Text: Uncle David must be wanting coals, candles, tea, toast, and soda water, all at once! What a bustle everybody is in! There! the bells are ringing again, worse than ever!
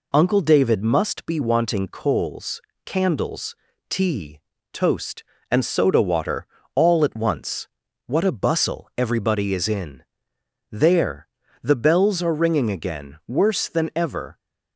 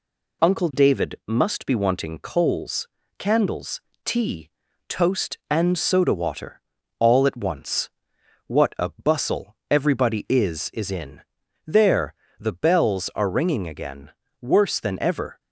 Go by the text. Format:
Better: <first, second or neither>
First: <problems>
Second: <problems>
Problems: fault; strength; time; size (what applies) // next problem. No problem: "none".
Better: first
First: none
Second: says "is" twice; at 10.7 s